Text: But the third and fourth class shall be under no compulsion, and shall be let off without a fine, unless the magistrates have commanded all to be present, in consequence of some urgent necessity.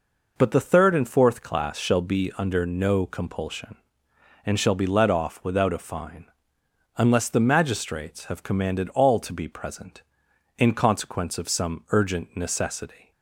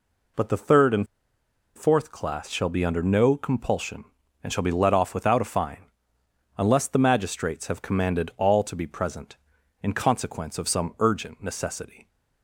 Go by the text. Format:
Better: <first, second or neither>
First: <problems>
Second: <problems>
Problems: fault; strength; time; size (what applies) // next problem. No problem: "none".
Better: first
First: none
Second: pauses between "and" and "fourth"; noticeable; at 1.0 s; 0.70 s long